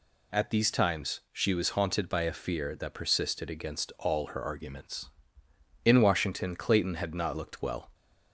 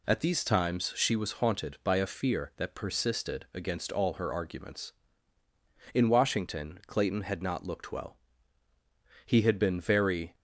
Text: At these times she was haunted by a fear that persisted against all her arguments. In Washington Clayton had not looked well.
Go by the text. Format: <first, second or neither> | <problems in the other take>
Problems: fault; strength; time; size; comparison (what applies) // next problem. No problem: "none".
first | goes on to say "He had been very"; noticeable; from 9.2 s on; 1.0 s long